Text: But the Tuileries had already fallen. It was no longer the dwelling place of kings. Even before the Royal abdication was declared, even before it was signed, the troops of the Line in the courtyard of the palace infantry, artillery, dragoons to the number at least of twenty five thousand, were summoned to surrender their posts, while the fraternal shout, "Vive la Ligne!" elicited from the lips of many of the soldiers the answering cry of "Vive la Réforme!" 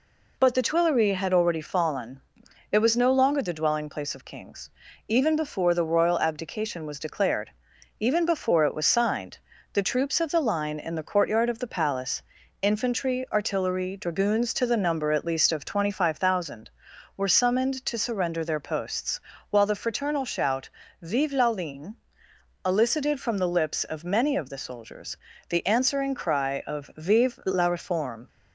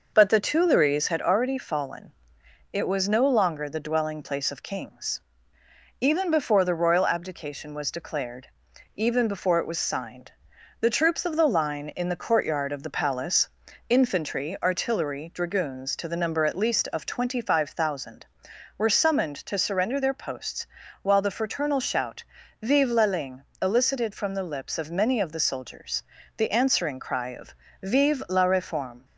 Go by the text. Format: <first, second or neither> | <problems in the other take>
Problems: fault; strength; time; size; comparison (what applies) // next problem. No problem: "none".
first | starts louder than the rest; noticeable; until 1.2 s; 5.5 dB // pauses between "palace" and "infantry"; at 13.4 s; 0.40 s long; also in the first // pauses between "soldiers" and "the"; slight; at 26.0 s; 0.34 s long; slight in the first // pauses between "of" and "Vive"; slight; at 27.5 s; 0.26 s long